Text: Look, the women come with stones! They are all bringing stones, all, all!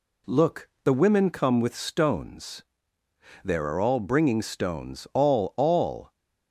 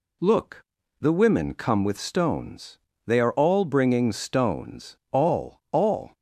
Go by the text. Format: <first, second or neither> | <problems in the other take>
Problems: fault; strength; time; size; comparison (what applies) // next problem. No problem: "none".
second | says "There" for "They"; at 3.4 s